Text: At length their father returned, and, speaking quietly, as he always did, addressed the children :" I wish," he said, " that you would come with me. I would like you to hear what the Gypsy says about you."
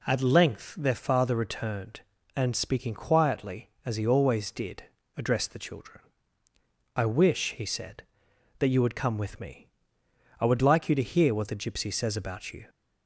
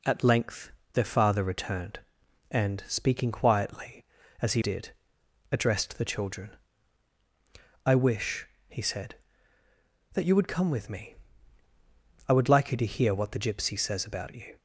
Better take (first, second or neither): first